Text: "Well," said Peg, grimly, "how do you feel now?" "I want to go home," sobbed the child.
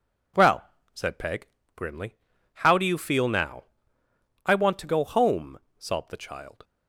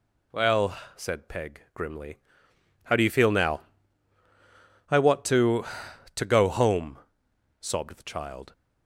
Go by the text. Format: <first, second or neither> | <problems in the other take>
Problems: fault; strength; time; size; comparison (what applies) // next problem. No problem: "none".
first | says "to" twice; at 6.1 s